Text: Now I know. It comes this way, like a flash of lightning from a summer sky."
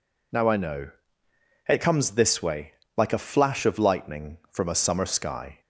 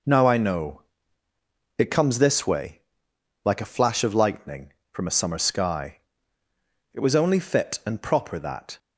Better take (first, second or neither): first